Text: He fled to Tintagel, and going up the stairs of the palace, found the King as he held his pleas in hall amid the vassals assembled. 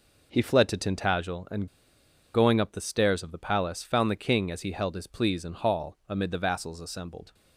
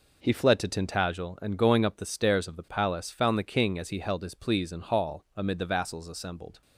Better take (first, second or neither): second